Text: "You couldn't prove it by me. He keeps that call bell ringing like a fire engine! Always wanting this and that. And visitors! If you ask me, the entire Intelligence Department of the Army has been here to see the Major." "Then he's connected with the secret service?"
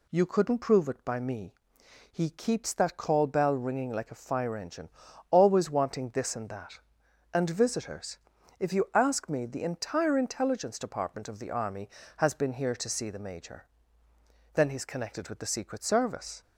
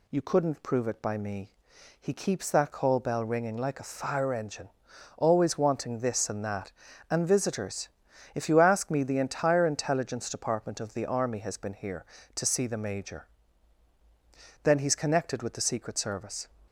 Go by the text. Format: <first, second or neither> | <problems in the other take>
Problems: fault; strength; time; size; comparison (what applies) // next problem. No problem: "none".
neither | none